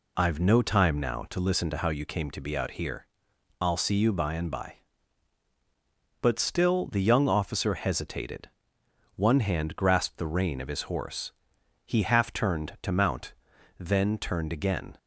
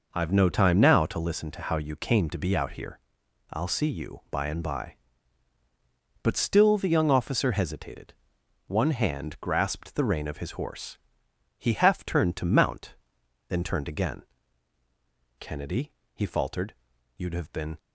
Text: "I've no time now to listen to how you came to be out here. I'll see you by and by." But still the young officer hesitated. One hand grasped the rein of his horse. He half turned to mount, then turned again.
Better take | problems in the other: first | goes on to say "Kennedy he faltered you'd have been"; strong; from 15.3 s on; 2.4 s long

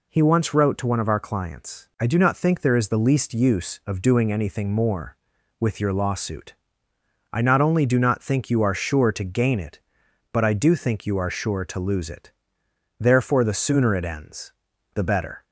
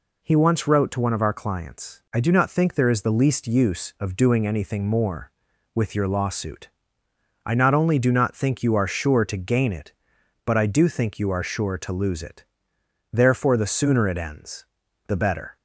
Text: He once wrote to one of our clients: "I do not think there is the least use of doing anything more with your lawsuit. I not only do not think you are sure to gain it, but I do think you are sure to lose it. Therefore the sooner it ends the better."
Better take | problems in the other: neither | pauses between "ends" and "the"; the same in both

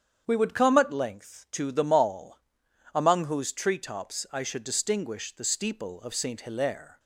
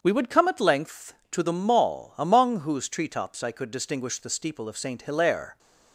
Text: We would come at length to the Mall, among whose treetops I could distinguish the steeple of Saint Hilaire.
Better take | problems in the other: second | starts louder than the rest; strong; until 1.2 s; 8 dB; strong in the second // says "should" for "could"; at 4.4 s

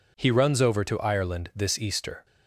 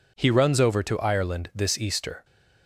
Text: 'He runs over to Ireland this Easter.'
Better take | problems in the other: neither | none

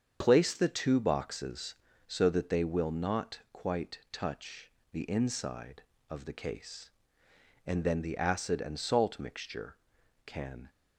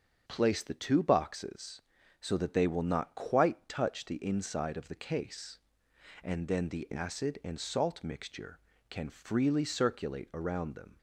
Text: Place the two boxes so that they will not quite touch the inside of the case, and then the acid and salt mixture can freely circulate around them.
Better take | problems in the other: second | starts louder than the rest; strong; until 1.2 s; 7.5 dB; strong in the second // pauses between "touch" and "the"; slight; at 4.6 s; 0.22 s long // stops before "freely circulate around them"; at 10.6 s

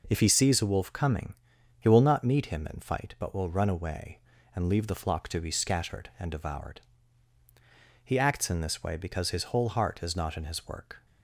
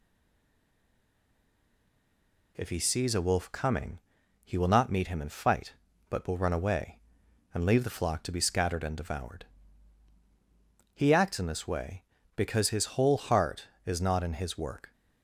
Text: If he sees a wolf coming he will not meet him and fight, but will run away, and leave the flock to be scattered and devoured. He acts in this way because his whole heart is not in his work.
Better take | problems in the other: first | stays silent before the first word; strong; until 2.5 s; 2.5 s long // pauses between "coming" and "he"; noticeable; at 3.9 s; 0.46 s long; noticeable in the first

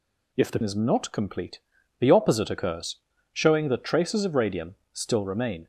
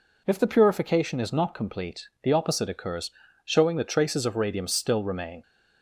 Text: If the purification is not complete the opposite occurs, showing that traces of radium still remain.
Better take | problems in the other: second | skips "purification"; at 0.6 s // pauses between "complete" and "the"; at 1.5 s; 0.40 s long; slight in the second // pauses between "radium" and "still"; slight; at 4.7 s; 0.16 s long

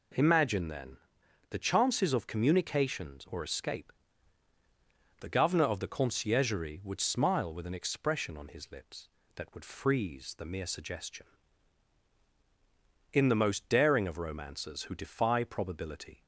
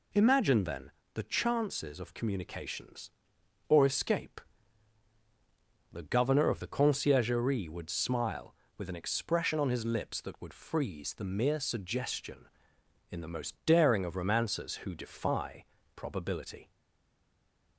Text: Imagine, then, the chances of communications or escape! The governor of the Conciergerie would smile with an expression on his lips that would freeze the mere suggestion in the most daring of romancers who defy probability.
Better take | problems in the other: first | pauses between "defy" and "probability"; slight; at 15.6 s; 0.30 s long // stays silent after the last word; from 16.7 s on; 1.0 s long

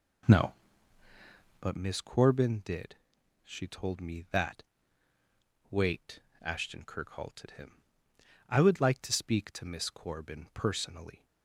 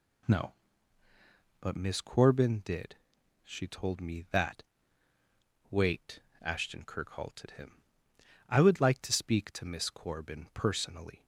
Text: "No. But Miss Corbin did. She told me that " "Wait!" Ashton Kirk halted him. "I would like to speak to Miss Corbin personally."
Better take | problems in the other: second | starts louder than the rest; noticeable; until 1.7 s; 4.5 dB

